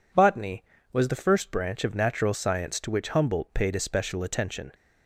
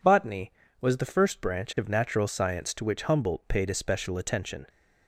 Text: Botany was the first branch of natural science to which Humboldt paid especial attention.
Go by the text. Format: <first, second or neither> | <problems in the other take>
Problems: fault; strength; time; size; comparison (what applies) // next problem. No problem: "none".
neither | none